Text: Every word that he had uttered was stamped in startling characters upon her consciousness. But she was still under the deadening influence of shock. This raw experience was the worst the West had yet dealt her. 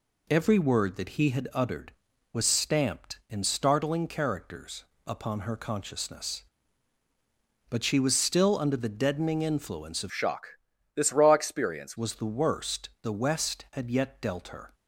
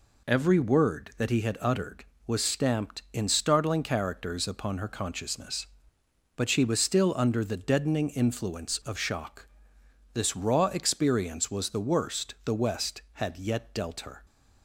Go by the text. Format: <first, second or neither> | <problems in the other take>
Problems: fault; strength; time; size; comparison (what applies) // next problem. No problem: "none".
second | pauses between "characters" and "upon"; slight; at 4.8 s; 0.22 s long // changes voice from "shock" to "experience"; from 10.1 to 11.9 s; 1.8 s long